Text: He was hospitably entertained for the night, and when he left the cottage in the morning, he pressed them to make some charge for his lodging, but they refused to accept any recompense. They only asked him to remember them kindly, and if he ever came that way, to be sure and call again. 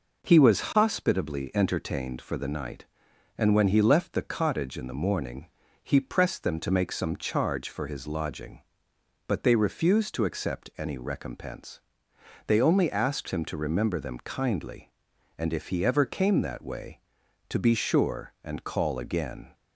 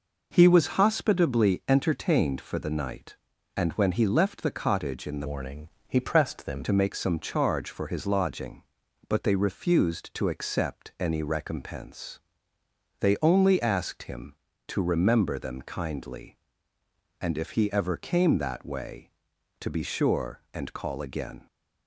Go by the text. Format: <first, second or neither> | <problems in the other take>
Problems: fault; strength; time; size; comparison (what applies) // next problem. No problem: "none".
first | changes voice from "morning" to "them"; from 5.2 to 6.6 s; 1.4 s long